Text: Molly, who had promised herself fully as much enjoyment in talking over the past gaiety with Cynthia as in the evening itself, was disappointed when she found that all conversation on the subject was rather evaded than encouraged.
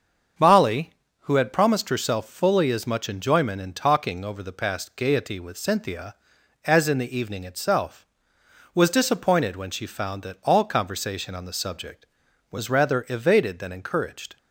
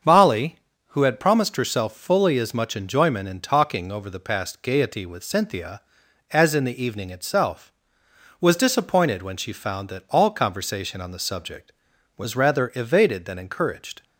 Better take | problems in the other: neither | starts louder than the rest; the same in both

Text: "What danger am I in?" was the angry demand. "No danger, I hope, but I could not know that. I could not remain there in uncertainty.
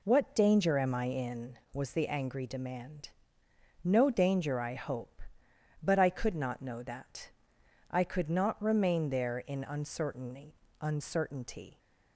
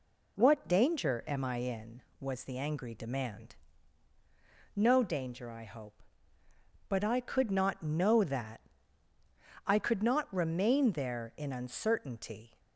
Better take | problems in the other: second | says "uncertainty" twice; at 10.7 s

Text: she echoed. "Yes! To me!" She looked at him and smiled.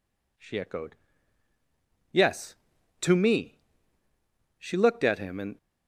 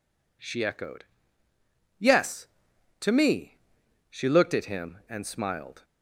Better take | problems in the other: second | stops before "smiled"; at 5.5 s

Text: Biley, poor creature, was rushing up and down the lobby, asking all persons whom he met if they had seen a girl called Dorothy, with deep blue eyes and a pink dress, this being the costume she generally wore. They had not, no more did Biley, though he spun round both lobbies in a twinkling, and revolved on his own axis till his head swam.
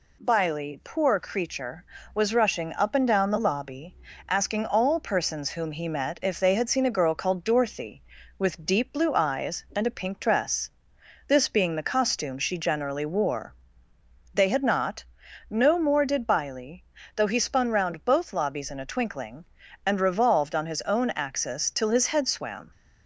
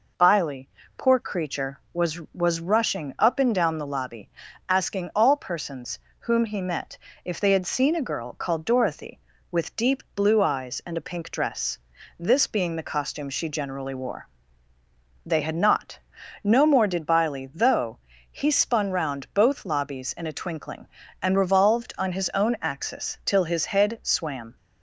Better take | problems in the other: first | says "was" twice; at 2.3 s // pauses between "persons" and "whom"; slight; at 5.9 s; 0.18 s long // pauses between "met" and "if"; slight; at 6.9 s; 0.26 s long // pauses between "though" and "he"; slight; at 17.9 s; 0.32 s long

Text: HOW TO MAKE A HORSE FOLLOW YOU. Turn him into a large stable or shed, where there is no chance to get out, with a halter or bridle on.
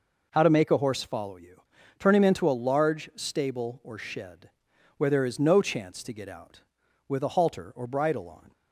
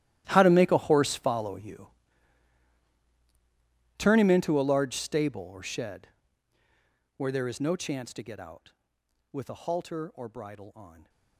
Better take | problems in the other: first | gets quieter; strong; throughout; 18.5 dB

